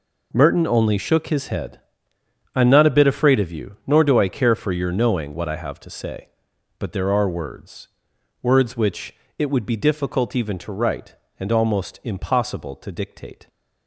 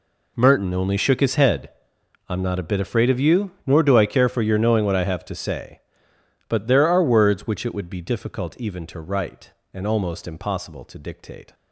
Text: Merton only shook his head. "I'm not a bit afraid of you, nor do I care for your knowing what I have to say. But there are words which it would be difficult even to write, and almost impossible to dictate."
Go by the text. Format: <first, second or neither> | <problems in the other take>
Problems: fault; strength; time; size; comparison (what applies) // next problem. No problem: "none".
second | says "words" twice; at 8.4 s // pauses between "which" and "it"; slight; at 9.1 s; 0.24 s long